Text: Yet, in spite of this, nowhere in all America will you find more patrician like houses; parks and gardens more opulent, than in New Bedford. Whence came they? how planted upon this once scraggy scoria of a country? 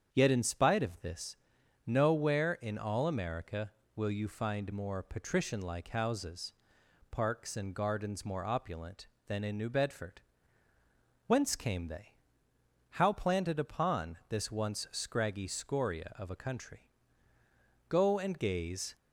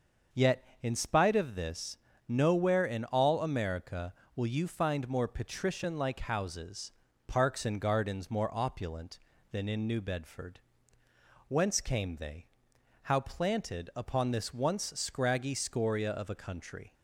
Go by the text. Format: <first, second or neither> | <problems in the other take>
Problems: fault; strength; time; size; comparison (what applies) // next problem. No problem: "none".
second | starts louder than the rest; strong; until 1.1 s; 8 dB; also in the second // goes on to say "Go and gaze"; noticeable; from 17.8 s on; 1.0 s long